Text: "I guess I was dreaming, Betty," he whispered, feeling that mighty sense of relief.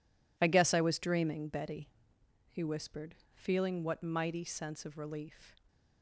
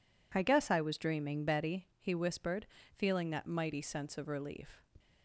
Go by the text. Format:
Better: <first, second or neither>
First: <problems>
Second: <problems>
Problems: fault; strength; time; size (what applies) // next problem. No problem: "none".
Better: second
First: says "what" for "that"; at 3.8 s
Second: none